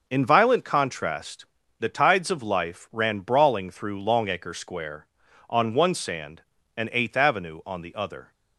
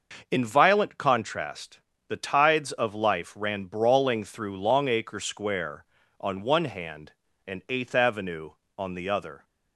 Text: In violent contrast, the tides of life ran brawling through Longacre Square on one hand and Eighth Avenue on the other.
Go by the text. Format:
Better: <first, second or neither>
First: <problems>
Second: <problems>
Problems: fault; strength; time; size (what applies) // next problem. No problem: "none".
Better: second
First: starts louder than the rest; until 1.0 s; 6 dB // says "sand" for "hand"; at 5.9 s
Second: starts louder than the rest; noticeable; until 1.3 s; 6 dB